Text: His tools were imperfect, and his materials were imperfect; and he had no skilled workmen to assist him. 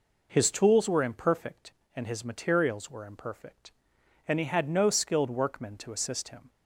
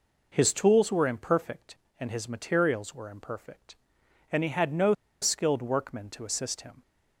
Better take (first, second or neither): first